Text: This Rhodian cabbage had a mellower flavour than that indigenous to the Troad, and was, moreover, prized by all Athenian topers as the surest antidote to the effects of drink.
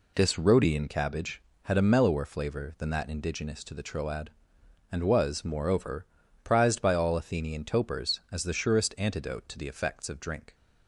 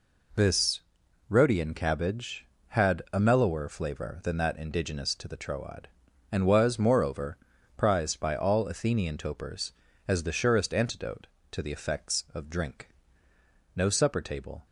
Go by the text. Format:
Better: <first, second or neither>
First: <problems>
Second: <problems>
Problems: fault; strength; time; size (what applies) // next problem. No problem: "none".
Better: first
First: none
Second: pauses between "This" and "Rhodian"; noticeable; at 0.7 s; 0.48 s long // goes on to say "No supper table"; noticeable; from 13.7 s on; 0.90 s long